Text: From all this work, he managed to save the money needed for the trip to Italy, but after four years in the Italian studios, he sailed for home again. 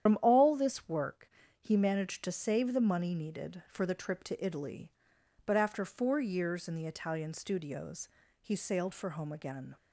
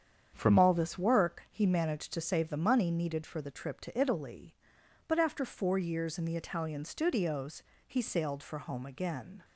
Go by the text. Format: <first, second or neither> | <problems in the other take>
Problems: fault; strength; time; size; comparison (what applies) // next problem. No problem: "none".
second | loses the start of "From"; at 0.0 s; 75 ms // starts louder than the rest; strong; until 1.1 s; 9.5 dB; strong in the second